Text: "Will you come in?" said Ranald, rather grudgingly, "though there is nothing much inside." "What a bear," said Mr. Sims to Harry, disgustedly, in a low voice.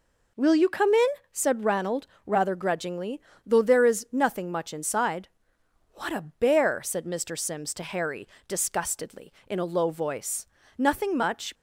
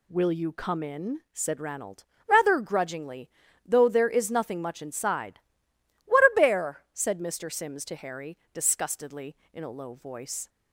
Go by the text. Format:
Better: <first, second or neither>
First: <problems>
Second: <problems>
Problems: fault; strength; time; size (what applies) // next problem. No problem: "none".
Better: second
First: goes on to say "Nothing much"; noticeable; from 10.7 s on; 0.78 s long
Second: none